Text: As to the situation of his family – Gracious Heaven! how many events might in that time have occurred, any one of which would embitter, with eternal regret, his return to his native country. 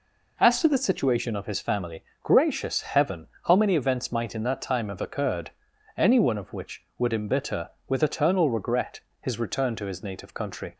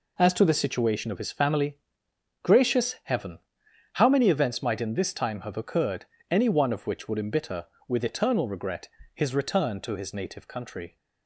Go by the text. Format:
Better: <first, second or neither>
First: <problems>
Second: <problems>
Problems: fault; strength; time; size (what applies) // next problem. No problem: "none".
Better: first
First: none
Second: says "this" for "that"; at 4.9 s